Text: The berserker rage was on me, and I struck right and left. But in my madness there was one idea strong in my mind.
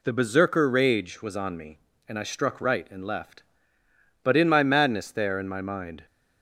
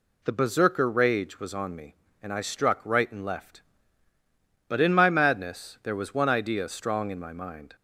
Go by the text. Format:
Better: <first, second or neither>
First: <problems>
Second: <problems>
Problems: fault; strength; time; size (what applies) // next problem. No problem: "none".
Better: second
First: skips "was one idea strong"; at 5.3 s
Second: none